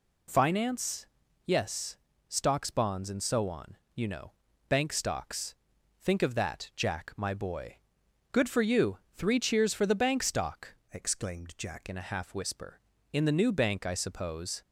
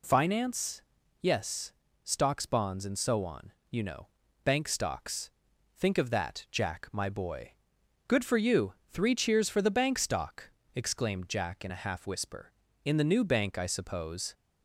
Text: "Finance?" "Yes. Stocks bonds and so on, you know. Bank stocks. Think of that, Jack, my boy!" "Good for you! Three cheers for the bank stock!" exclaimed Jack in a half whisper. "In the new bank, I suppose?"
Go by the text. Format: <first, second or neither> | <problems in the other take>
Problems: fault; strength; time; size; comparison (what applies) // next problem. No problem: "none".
second | changes voice from "exclaimed" to "Jack"; from 10.9 to 11.8 s; 0.9 s long